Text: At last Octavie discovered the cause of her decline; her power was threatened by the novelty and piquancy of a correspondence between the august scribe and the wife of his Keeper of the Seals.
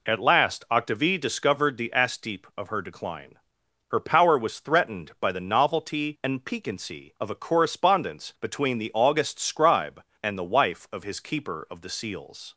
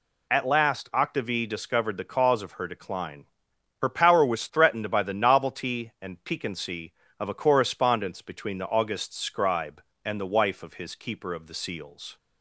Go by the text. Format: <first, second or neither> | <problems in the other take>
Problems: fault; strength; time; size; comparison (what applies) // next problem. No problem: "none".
second | says "asteep" for "cause"; at 1.9 s